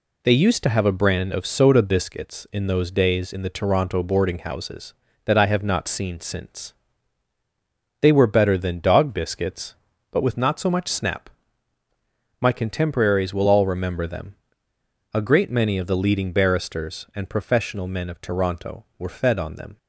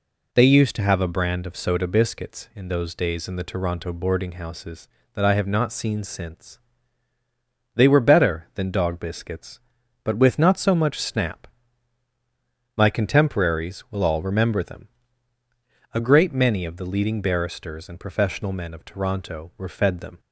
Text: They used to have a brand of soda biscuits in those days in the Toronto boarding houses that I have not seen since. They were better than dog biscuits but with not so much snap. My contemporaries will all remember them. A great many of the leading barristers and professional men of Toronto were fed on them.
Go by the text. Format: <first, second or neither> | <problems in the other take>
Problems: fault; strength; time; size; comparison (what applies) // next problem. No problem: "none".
first | skips "on"; at 19.9 s